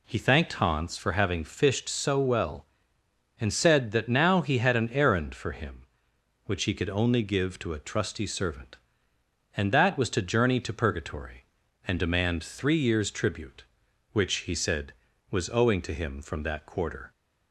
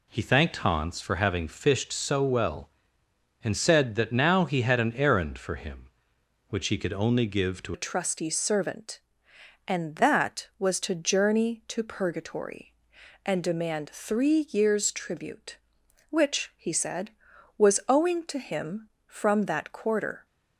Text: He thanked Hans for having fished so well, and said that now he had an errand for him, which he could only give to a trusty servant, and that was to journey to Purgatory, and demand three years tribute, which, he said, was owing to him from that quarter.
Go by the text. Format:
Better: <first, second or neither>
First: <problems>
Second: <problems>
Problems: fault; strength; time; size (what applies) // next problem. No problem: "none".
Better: first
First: none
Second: changes voice at "a"; from 7.7 s on; 12.5 s long